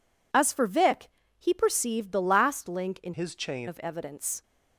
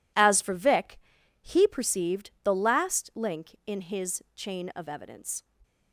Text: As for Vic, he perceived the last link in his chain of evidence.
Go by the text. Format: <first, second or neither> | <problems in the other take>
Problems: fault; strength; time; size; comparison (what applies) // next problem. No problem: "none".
second | changes voice from "his" to "chain"; from 3.1 to 3.6 s; 0.5 s long